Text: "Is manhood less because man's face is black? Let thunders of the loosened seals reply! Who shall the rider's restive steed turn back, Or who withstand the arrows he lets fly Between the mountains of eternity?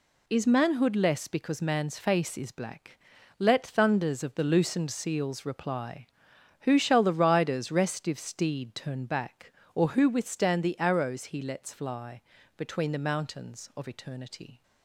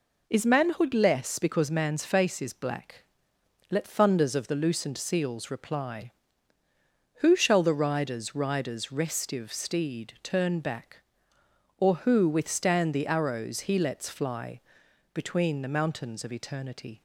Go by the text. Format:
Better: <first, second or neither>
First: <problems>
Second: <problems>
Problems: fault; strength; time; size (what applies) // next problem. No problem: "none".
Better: first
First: pauses between "fly" and "Between"; slight; at 12.2 s; 0.34 s long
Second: says "rider's" twice; at 8.3 s // pauses between "fly" and "Between"; noticeable; at 14.6 s; 0.50 s long